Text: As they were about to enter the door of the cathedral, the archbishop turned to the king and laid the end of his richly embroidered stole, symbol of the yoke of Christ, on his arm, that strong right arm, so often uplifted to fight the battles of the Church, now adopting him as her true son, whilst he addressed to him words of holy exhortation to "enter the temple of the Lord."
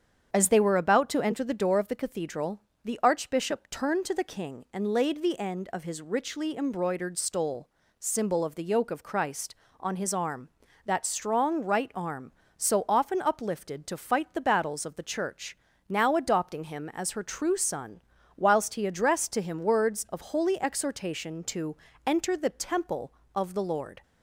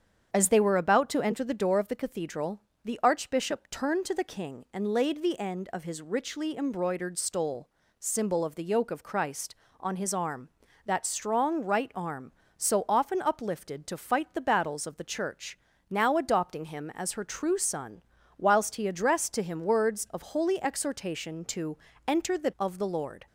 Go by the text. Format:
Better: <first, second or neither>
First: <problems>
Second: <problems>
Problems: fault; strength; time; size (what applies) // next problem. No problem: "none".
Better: first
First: starts louder than the rest; strong; until 1.3 s; 8 dB // pauses between "to" and "enter"; slight; at 21.7 s; 0.30 s long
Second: starts louder than the rest; strong; until 1.3 s; 8 dB // pauses between "to" and "enter"; slight; at 21.7 s; 0.30 s long // skips "temple"; at 22.5 s